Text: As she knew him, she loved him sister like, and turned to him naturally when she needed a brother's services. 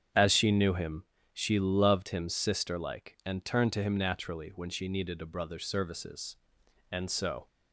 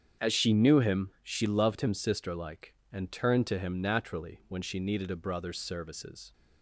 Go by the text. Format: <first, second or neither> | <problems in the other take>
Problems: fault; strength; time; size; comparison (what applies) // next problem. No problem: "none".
second | starts louder than the rest; strong; until 1.4 s; 8 dB; strong in the second // goes on to say "And so"; from 6.9 s on; 0.56 s long